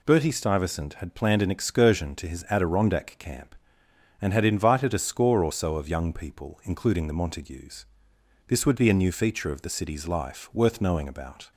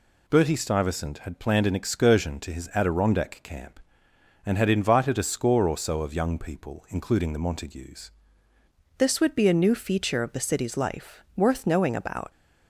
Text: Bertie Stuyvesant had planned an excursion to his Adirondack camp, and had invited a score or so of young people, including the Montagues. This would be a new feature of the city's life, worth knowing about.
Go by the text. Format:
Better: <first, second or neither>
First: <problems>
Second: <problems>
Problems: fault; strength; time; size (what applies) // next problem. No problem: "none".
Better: first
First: none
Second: changes voice at "This"; from 8.9 s on; 3.4 s long